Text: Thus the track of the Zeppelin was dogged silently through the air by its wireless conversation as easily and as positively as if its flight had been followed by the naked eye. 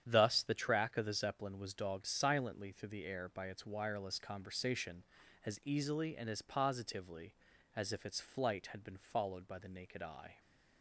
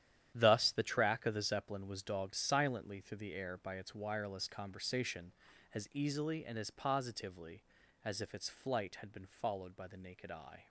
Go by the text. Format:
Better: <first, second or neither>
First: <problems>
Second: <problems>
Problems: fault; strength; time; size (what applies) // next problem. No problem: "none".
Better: first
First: starts louder than the rest; strong; until 1.0 s; 9 dB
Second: gets quieter; strong; throughout; 12 dB // starts louder than the rest; strong; until 1.3 s; 10.5 dB